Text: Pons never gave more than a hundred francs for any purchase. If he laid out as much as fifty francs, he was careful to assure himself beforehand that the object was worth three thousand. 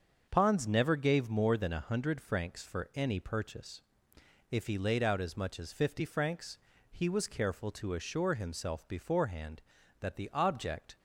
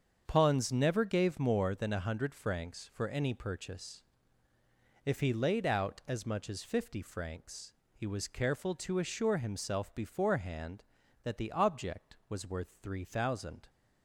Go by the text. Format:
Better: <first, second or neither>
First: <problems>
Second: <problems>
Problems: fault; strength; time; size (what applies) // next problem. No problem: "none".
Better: second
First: starts louder than the rest; until 1.3 s; 6.5 dB // stops before "was worth three thousand"; at 10.9 s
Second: starts louder than the rest; strong; until 1.2 s; 7 dB